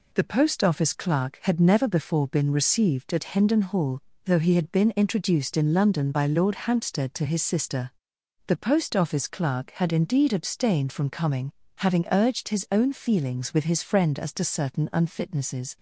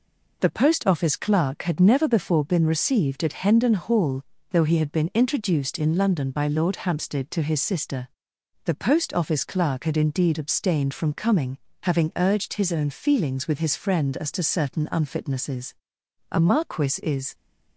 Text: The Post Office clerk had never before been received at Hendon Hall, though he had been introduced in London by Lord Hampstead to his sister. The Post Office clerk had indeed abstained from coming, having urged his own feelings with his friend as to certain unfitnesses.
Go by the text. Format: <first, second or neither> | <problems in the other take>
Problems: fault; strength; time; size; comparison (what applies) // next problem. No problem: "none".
first | goes on to say "A Marquis is"; noticeable; from 16.3 s on; 1.0 s long